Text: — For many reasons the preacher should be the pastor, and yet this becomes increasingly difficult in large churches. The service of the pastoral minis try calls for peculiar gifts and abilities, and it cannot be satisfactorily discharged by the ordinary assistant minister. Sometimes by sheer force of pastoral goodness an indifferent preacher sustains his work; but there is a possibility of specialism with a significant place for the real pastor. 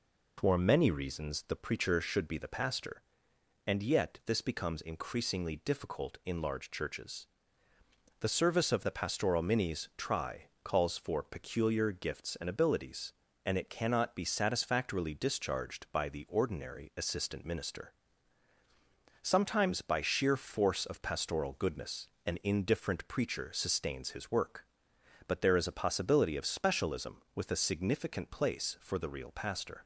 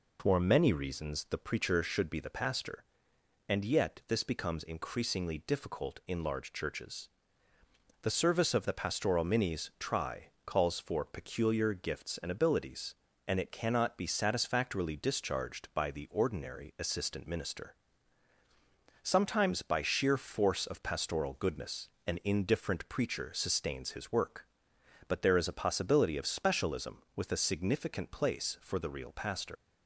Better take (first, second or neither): first